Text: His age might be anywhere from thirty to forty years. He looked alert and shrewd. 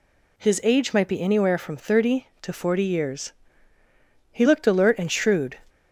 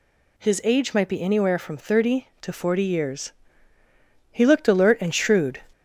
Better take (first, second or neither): first